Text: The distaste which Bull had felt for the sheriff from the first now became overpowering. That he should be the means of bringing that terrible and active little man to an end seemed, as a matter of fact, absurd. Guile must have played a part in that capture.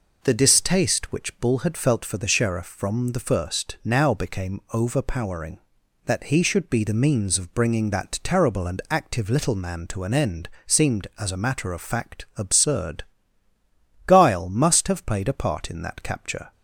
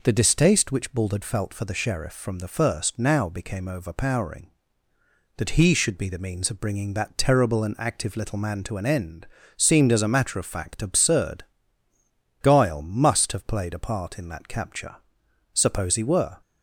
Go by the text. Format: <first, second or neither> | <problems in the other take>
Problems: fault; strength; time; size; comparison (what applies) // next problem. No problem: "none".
first | pauses between "end" and "seemed"; slight; at 9.2 s; 0.30 s long; slight in the first // goes on to say "Suppose he were"; noticeable; from 15.5 s on; 0.88 s long